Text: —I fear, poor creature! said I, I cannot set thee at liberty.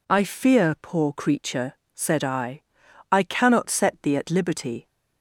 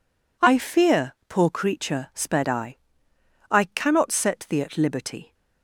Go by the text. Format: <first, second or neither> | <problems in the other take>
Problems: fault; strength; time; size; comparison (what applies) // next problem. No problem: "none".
first | says "sped" for "said"; at 2.1 s